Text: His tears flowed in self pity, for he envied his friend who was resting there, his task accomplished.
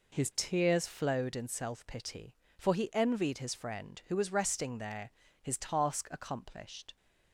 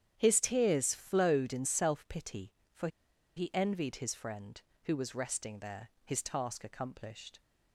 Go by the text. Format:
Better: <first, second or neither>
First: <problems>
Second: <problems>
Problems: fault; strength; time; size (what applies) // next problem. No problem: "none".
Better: first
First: none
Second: starts louder than the rest; strong; until 1.1 s; 9.5 dB // pauses between "for" and "he"; noticeable; at 2.8 s; 0.48 s long